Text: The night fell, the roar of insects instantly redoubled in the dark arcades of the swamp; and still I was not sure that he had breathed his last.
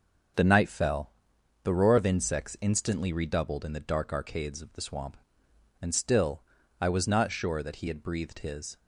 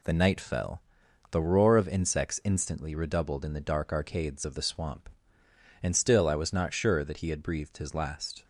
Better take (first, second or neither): second